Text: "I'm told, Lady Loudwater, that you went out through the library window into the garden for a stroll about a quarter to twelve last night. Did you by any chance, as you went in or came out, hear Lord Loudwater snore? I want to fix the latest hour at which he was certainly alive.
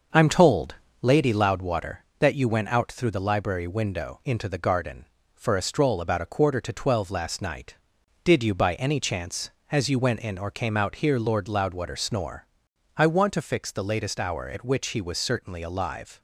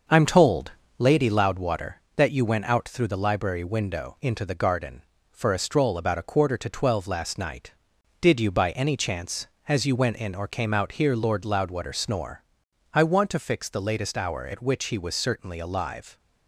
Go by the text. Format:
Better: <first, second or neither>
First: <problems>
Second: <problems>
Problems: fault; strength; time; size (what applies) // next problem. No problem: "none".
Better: neither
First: starts louder than the rest; until 1.3 s; 6 dB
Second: starts louder than the rest; until 1.3 s; 6 dB